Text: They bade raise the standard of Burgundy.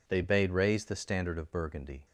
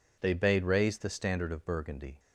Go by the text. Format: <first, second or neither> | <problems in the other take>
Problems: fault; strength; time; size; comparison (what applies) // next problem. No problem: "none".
neither | none